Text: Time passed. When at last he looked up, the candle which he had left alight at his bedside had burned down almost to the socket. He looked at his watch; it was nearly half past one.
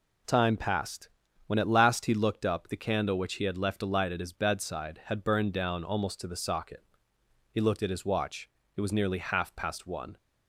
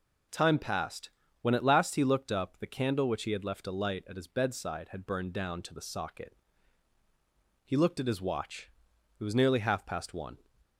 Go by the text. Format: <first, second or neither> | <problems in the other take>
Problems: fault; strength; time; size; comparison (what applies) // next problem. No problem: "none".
first | skips "almost"; at 5.6 s